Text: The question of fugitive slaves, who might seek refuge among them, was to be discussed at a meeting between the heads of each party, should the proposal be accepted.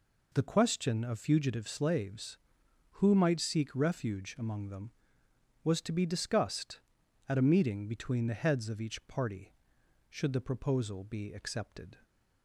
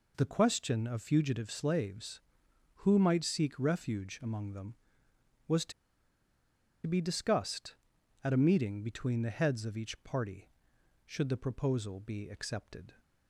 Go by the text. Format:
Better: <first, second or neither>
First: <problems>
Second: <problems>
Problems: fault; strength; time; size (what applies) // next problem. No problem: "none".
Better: first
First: none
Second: pauses between "to" and "be"; at 5.7 s; 1.1 s long